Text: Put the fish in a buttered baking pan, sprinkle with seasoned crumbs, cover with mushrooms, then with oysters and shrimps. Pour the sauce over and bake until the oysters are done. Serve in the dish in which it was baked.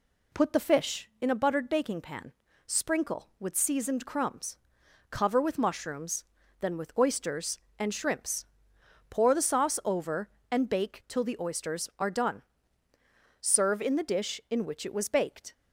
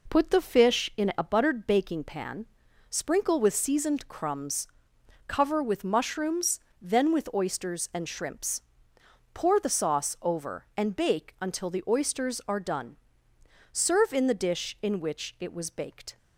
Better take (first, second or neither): second